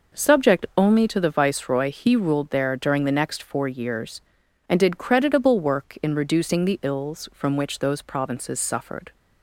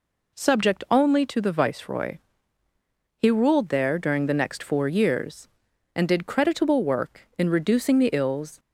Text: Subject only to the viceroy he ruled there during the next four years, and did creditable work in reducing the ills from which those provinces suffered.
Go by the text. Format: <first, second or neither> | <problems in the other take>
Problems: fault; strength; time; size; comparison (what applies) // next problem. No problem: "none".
first | pauses between "viceroy" and "he"; at 2.1 s; 1.0 s long // stops before "from which those provinces suffered"; at 8.5 s